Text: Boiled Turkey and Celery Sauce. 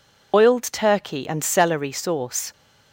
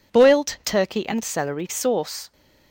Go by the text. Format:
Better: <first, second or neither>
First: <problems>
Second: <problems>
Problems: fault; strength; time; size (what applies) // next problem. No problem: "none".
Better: second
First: loses the start of "Boiled"; at 0.3 s; 90 ms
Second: none